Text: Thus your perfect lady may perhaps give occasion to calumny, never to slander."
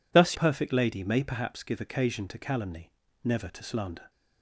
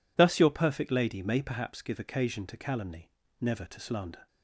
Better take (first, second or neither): second